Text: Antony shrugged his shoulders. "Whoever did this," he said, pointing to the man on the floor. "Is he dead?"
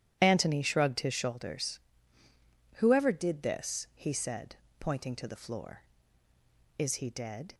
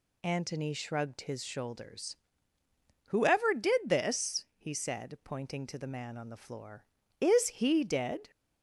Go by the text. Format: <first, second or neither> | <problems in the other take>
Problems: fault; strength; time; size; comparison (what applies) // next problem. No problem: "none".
second | starts louder than the rest; strong; until 1.2 s; 11.5 dB // skips "man on the"; at 5.3 s